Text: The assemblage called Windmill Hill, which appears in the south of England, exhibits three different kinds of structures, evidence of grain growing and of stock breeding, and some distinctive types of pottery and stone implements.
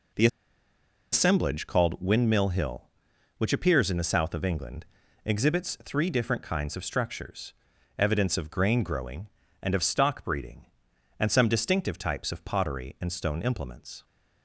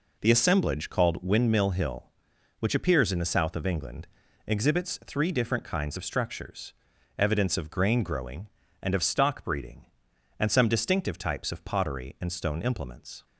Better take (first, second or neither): second